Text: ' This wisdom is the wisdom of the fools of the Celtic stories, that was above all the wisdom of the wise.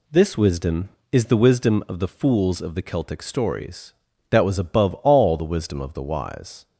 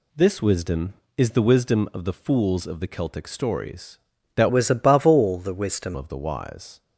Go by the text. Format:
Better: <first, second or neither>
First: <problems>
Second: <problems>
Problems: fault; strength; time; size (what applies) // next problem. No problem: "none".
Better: first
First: none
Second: changes voice from "was" to "wisdom"; from 4.4 to 5.9 s; 1.5 s long